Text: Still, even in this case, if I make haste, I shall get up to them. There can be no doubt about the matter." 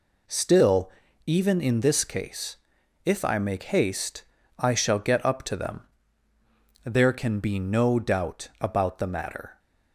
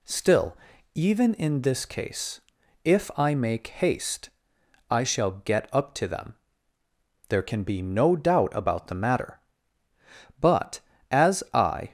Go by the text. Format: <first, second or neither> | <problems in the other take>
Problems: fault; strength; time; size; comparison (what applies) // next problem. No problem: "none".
first | goes on to say "But as I"; from 10.4 s on; 1.5 s long